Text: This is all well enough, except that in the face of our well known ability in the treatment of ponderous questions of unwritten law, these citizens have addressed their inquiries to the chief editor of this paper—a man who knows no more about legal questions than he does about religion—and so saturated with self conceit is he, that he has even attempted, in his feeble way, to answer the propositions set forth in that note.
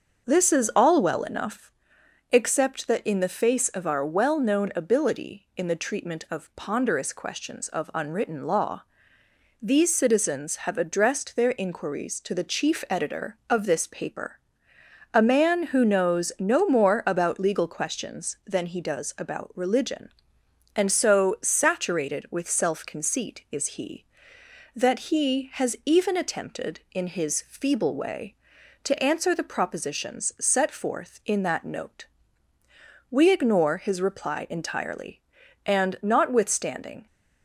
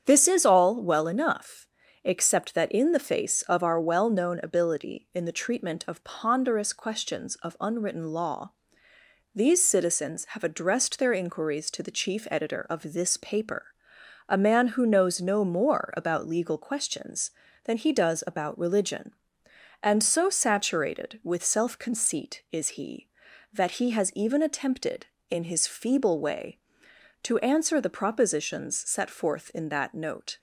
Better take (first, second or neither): second